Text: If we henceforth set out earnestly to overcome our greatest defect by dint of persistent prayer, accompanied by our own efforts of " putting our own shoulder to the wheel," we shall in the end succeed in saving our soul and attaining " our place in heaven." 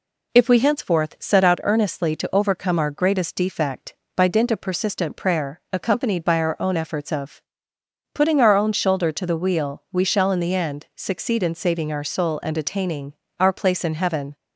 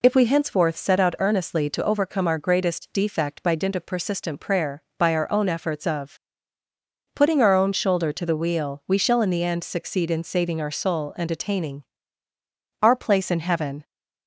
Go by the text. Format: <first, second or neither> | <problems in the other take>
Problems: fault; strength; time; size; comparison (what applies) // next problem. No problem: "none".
first | skips "accompanied"; at 4.9 s